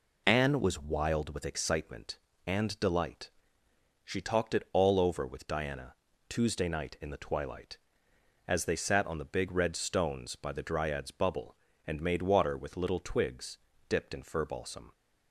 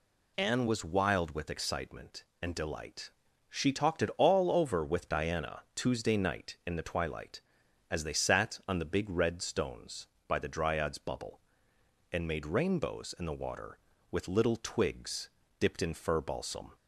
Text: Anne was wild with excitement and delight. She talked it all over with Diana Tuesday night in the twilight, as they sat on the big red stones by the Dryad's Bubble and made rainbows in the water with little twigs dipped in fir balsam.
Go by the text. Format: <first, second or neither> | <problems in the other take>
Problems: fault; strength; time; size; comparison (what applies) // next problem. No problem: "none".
second | pauses between "Diana" and "Tuesday"; slight; at 5.9 s; 0.34 s long // skips "rainbows in the"; at 12.2 s // pauses between "twigs" and "dipped"; slight; at 13.5 s; 0.30 s long; slight in the second